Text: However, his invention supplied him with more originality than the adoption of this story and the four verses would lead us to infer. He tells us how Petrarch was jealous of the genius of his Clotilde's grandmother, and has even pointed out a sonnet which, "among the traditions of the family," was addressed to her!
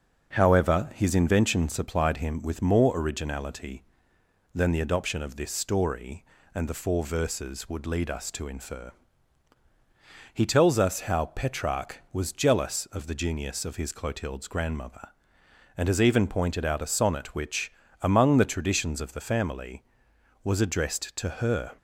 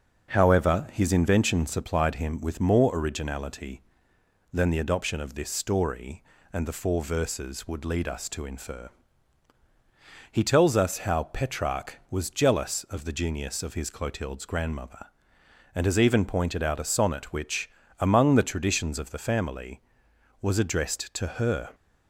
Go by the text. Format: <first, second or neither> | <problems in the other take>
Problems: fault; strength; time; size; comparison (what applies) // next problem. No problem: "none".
neither | starts louder than the rest; noticeable; the same in both